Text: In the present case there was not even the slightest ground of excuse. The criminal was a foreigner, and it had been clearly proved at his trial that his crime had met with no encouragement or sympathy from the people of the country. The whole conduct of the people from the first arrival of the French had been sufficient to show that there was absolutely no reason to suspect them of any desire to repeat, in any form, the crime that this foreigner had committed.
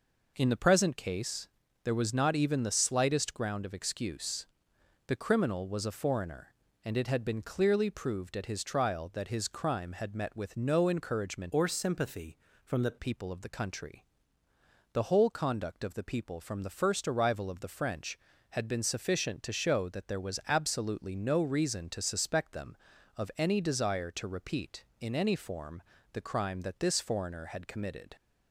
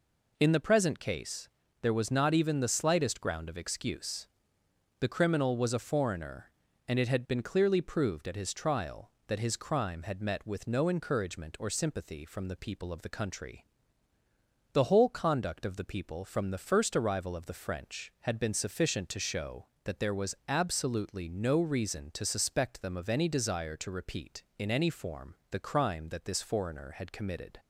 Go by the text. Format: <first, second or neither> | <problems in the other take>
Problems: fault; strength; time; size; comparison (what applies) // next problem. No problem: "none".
second | pauses between "case" and "there"; slight; at 1.4 s; 0.36 s long; slight in the second // changes voice from "or" to "the"; from 11.5 to 12.9 s; 1.4 s long